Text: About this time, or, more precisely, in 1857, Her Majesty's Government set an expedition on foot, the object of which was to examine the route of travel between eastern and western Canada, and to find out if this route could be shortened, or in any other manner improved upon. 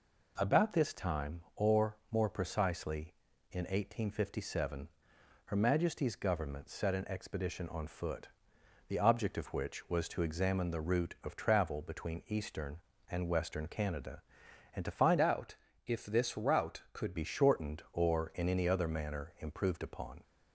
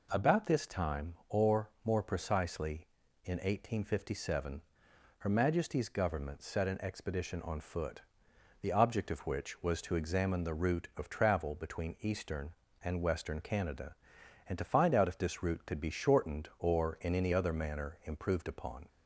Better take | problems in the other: second | changes voice from "out" to "could"; from 15.1 to 17.1 s; 2.0 s long // pauses between "out" and "if"; slight; at 15.5 s; 0.28 s long

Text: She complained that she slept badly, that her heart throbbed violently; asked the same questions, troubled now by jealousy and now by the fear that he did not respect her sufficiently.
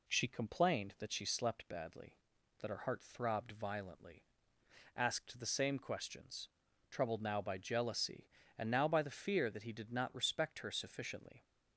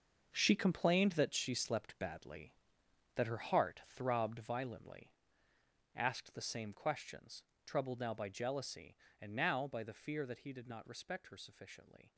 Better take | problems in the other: first | gets quieter; strong; throughout; 12 dB

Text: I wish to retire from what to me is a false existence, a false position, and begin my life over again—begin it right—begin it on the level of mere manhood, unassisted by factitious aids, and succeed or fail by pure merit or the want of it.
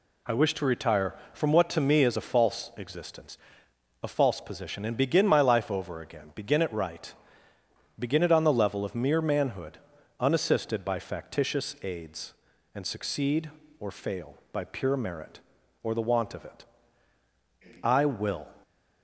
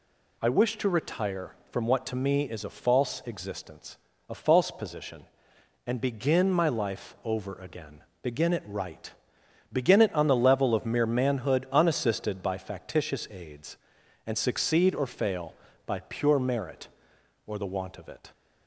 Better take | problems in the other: second | goes on to say "I will"; noticeable; from 17.8 s on; 0.64 s long

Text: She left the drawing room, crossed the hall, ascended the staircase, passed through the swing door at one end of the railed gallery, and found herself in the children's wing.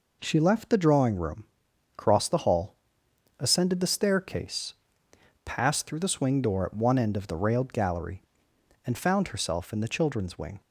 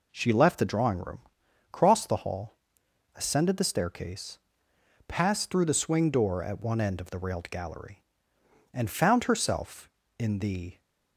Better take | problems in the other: first | stops before "children's wing"; at 10.8 s

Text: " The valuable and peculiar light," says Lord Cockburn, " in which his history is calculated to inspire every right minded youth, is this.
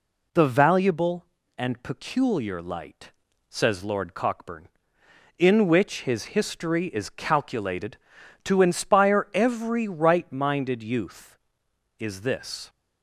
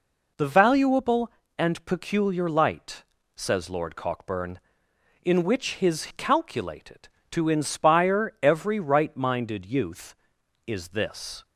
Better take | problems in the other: first | skips "history is"; at 6.1 s

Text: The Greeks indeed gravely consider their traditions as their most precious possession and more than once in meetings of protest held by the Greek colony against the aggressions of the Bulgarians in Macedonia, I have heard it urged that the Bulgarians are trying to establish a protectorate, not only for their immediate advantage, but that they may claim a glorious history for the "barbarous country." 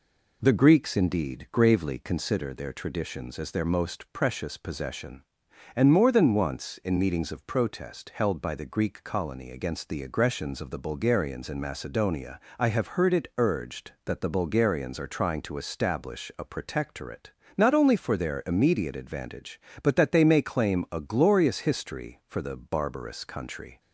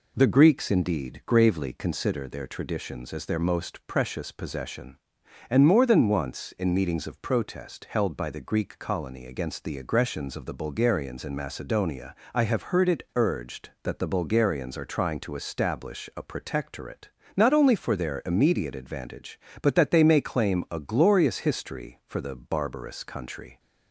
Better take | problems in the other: neither | none

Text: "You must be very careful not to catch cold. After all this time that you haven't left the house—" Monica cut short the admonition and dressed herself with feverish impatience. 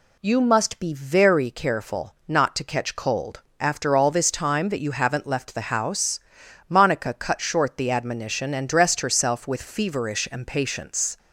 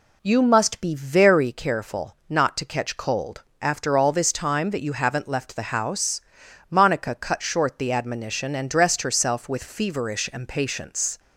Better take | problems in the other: first | starts louder than the rest; slight; until 1.6 s; 2 dB

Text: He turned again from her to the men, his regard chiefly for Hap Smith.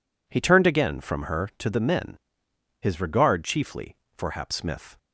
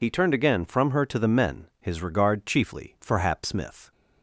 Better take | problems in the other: first | loses the start of "He"; at 0.0 s; 45 ms

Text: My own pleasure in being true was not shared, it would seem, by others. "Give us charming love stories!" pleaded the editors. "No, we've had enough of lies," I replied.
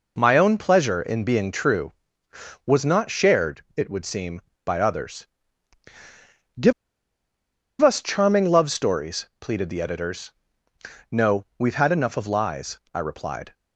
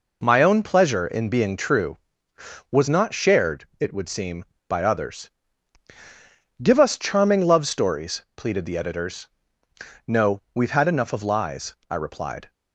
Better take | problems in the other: second | pauses between "Give" and "us"; at 6.7 s; 1.0 s long

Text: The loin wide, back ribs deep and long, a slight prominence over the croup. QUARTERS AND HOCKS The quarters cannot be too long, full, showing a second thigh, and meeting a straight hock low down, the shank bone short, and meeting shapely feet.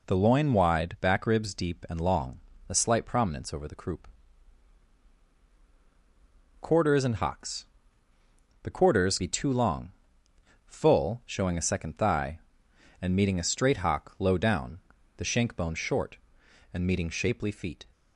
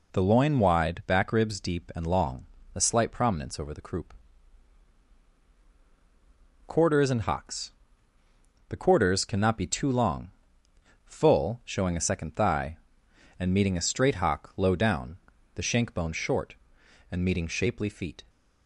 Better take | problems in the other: second | pauses between "HOCKS" and "The"; noticeable; at 7.6 s; 0.96 s long; noticeable in the second // skips "cannot"; at 9.1 s

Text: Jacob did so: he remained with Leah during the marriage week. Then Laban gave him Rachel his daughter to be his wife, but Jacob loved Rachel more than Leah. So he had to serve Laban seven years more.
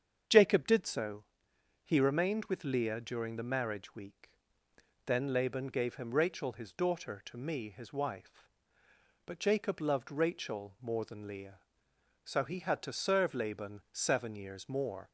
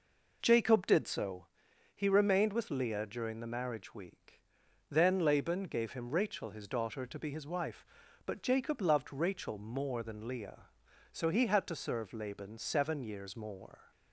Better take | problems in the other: second | starts louder than the rest; strong; until 1.9 s; 7.5 dB // says "me" for "be"; at 7.3 s

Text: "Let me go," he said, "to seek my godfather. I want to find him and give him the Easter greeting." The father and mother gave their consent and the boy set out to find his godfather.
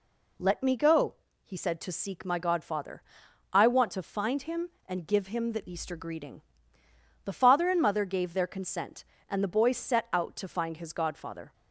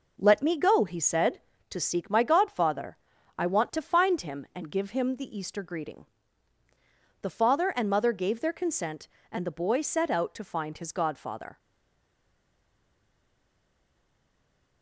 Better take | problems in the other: first | stays silent after the last word; strong; from 11.5 s on; 3.3 s long

